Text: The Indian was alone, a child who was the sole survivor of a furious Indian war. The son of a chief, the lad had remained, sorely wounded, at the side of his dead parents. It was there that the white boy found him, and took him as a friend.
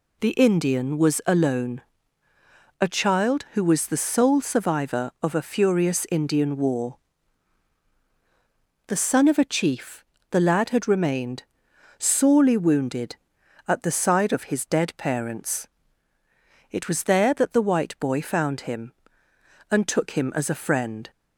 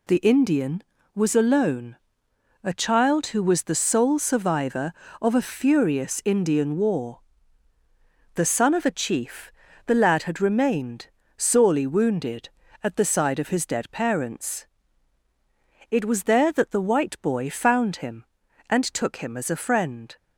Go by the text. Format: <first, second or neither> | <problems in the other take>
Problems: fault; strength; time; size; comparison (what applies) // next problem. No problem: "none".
neither | none